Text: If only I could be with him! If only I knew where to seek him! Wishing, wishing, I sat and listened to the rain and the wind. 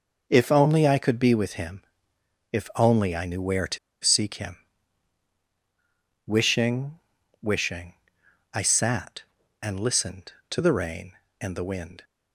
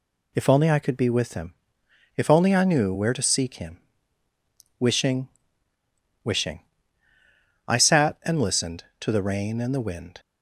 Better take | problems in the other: second | pauses between "to" and "seek"; slight; at 3.7 s; 0.25 s long

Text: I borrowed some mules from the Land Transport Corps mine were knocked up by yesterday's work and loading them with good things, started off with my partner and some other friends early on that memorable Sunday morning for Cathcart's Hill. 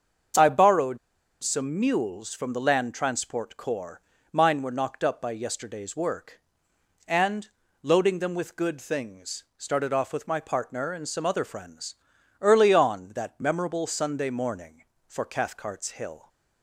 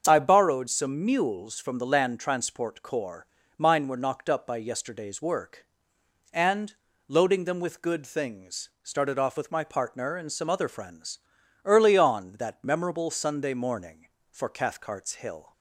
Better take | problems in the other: second | starts louder than the rest; until 1.8 s; 7 dB; also in the second // pauses between "borrowed" and "some"; noticeable; at 0.9 s; 0.46 s long // pauses between "Corps" and "mine"; slight; at 4.0 s; 0.30 s long; slight in the second // pauses between "and" and "loading"; slight; at 7.4 s; 0.34 s long; slight in the second // pauses between "friends" and "early"; noticeable; at 11.9 s; 0.46 s long; noticeable in the second

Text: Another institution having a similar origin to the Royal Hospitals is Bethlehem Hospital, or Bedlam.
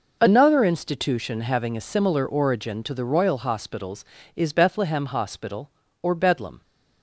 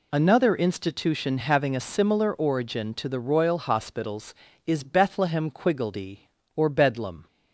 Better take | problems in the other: first | says "Quiggledy" for "Hospital"; at 5.5 s

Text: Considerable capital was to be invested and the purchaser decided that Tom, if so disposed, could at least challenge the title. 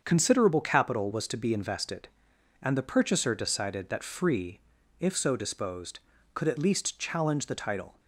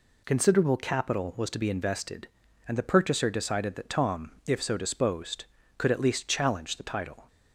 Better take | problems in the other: second | starts louder than the rest; until 1.0 s; 7 dB // says "Free" for "Tom"; at 4.0 s

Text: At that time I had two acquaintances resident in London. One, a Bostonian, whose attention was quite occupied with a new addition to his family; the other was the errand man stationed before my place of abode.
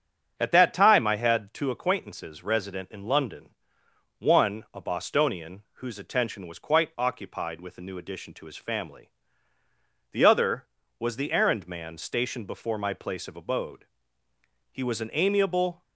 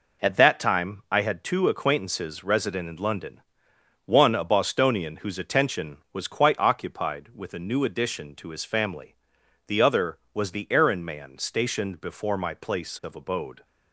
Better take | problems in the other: second | starts louder than the rest; strong; until 1.3 s; 7 dB // goes on to say "He was an amiable"; noticeable; from 14.7 s on; 1.1 s long

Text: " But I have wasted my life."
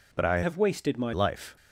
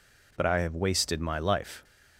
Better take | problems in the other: second | changes voice from "have" to "my"; from 0.4 to 1.1 s; 0.7 s long

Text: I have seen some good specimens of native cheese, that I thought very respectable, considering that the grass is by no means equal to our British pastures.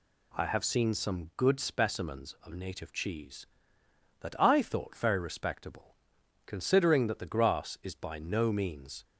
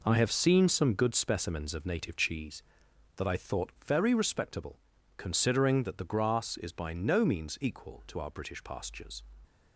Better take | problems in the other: second | stops before "equal to our British pastures"; at 9.0 s

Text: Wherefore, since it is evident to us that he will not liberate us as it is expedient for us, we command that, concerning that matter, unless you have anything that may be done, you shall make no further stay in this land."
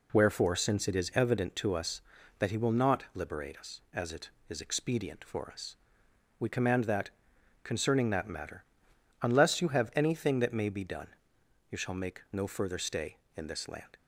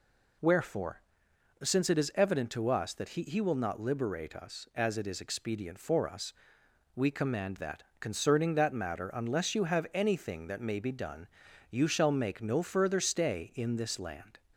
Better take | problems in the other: first | says "he" twice; at 3.2 s

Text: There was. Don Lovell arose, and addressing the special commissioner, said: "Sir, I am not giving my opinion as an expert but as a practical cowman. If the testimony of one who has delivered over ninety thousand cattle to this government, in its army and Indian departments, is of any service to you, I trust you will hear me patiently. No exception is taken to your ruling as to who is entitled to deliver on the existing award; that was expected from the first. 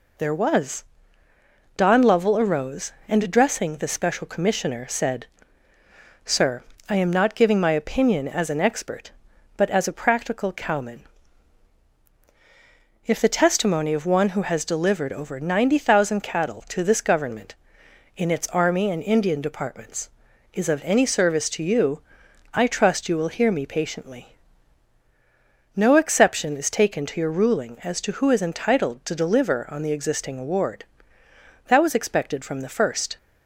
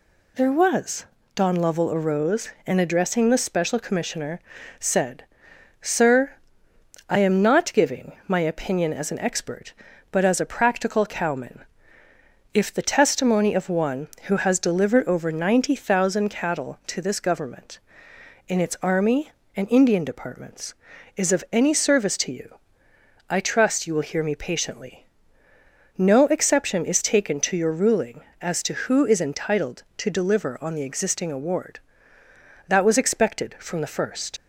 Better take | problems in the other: first | leaves "first" unfinished; at 34.3 s; 55 ms

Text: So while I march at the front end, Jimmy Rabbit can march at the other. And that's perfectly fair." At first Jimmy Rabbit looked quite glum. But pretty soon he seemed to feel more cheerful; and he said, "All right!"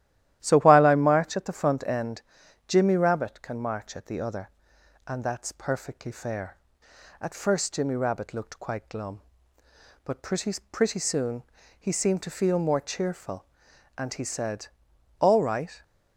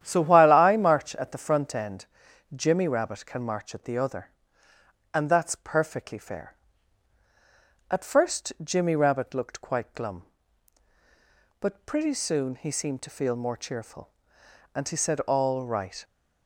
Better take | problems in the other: second | starts louder than the rest; strong; until 1.4 s; 13 dB; strong in the second // says "pretty" twice; at 10.7 s // pauses between "soon" and "he"; slight; at 11.4 s; 0.36 s long

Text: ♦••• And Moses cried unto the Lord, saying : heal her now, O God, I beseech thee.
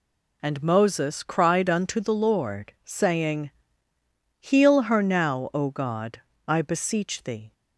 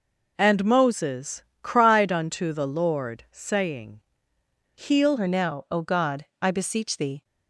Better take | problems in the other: first | pauses between "Moses" and "cried"; slight; at 1.4 s; 0.20 s long // changes voice at "her"; from 5.1 s on; 2.1 s long

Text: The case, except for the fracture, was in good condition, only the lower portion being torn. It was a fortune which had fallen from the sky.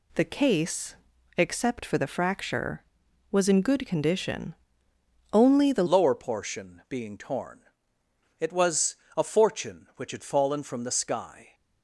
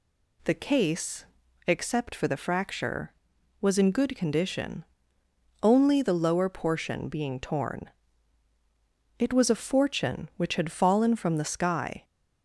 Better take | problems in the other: second | changes voice at "lower"; from 5.8 s on; 5.7 s long // pauses between "was" and "a"; slight; at 8.9 s; 0.22 s long

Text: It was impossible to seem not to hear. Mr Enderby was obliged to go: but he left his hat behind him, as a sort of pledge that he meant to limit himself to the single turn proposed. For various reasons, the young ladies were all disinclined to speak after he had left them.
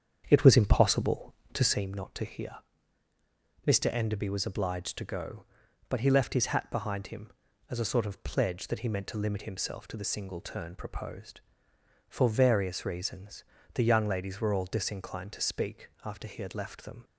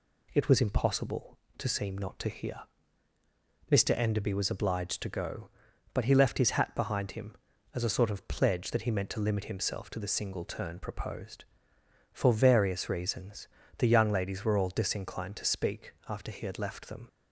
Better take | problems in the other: second | starts louder than the rest; strong; until 1.9 s; 8 dB // pauses between "speak" and "after"; slight; at 15.8 s; 0.16 s long; slight in the second

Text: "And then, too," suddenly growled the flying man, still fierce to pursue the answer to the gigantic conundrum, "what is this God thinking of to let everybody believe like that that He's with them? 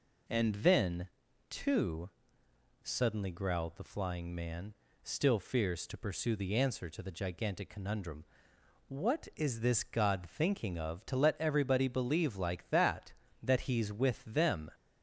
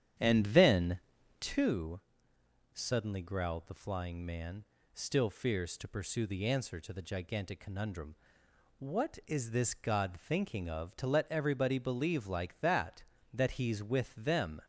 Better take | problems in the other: first | starts louder than the rest; strong; until 1.8 s; 9.5 dB

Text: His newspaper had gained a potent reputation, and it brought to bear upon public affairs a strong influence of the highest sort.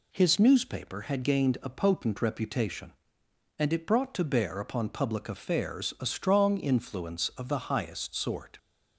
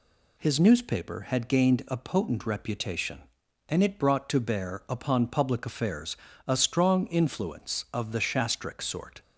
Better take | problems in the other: first | pauses between "affairs" and "a"; slight; at 6.1 s; 0.32 s long // says "shastric" for "highest"; at 8.2 s

